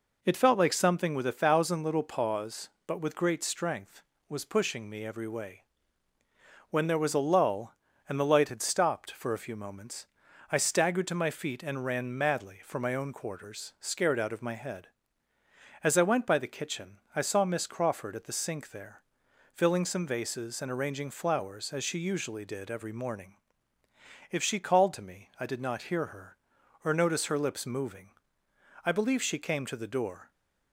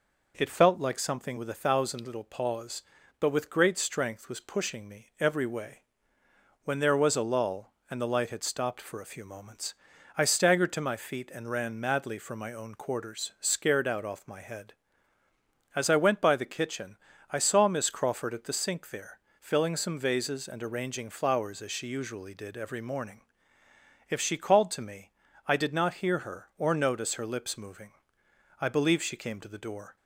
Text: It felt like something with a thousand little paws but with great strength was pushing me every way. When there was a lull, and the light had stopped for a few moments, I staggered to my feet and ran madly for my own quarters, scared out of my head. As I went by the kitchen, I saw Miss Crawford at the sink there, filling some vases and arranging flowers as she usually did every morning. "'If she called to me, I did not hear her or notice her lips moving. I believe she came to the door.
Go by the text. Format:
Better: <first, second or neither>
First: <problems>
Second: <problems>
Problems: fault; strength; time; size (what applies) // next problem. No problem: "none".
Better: first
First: none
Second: says "off" for "of"; at 14.0 s